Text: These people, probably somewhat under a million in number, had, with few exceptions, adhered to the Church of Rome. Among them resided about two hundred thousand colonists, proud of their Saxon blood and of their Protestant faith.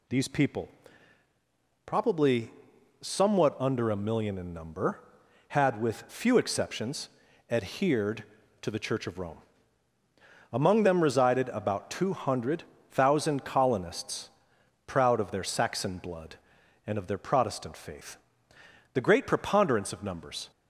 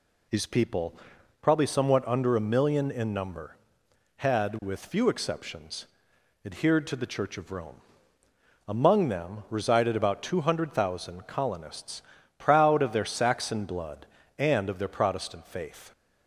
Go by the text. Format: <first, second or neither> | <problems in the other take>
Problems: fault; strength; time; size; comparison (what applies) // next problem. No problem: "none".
second | pauses between "probably" and "somewhat"; noticeable; at 2.5 s; 0.50 s long // pauses between "hundred" and "thousand"; slight; at 12.6 s; 0.28 s long // goes on to say "The great preponderance of numbers"; from 18.9 s on; 1.5 s long